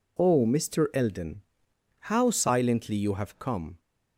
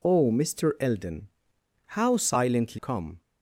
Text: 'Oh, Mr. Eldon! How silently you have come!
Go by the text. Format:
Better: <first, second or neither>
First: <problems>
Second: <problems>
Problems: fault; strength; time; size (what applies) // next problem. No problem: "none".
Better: first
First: none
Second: skips "you have"; at 2.7 s